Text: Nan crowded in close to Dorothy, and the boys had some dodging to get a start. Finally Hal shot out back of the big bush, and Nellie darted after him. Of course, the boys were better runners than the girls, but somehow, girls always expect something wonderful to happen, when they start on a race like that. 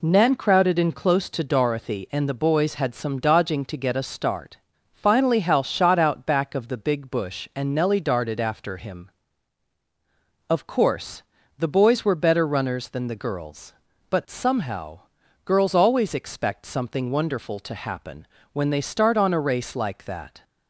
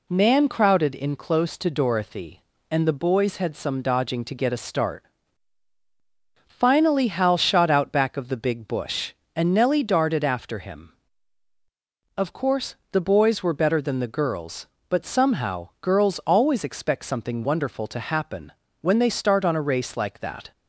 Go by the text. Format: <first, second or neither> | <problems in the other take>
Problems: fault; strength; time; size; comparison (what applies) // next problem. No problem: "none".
first | skips "runners"; at 13.8 s